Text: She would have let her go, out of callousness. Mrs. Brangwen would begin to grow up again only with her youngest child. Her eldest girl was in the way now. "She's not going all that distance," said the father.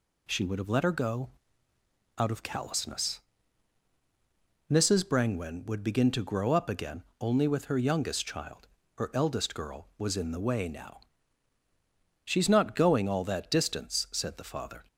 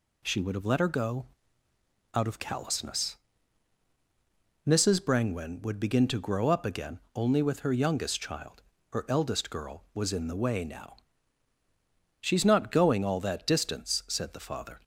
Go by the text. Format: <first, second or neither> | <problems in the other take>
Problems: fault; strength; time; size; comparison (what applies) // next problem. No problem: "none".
neither | pauses between "again" and "only"; slight; the same in both